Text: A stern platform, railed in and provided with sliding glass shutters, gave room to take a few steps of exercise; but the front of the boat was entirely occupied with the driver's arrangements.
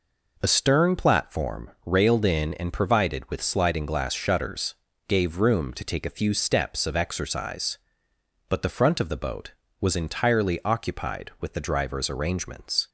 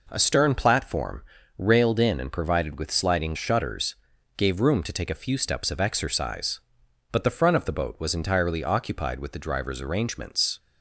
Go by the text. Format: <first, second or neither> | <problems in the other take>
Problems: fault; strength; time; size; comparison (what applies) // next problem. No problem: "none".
first | skips "glass"; at 3.3 s